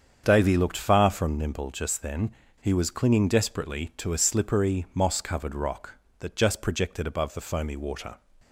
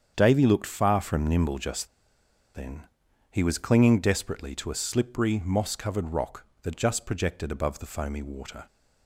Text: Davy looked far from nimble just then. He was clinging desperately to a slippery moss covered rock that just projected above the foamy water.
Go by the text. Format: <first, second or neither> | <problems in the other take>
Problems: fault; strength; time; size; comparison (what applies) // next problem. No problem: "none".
first | starts louder than the rest; strong; until 1.1 s; 8 dB; strong in the first // pauses between "just" and "then"; noticeable; at 1.8 s; 0.68 s long